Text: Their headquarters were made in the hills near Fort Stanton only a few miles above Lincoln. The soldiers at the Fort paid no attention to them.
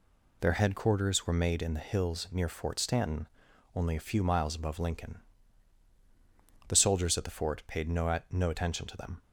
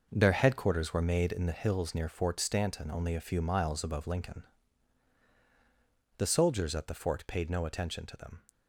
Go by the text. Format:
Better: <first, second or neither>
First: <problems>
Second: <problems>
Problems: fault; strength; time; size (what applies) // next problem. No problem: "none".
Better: second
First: pauses between "Stanton" and "only"; noticeable; at 3.2 s; 0.46 s long // says "no" twice; at 8.2 s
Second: none